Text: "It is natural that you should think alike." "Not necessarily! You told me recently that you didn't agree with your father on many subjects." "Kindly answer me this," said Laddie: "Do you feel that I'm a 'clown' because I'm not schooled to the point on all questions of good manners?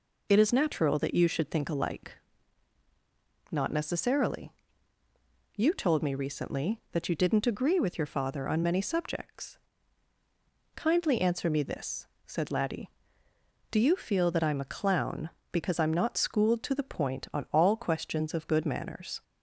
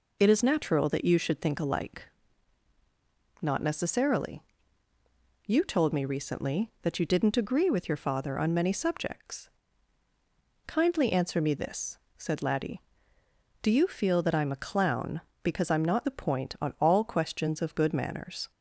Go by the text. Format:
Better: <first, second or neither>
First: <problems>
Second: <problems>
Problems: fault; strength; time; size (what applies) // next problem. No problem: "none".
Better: first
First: none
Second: skips "schooled to"; at 16.0 s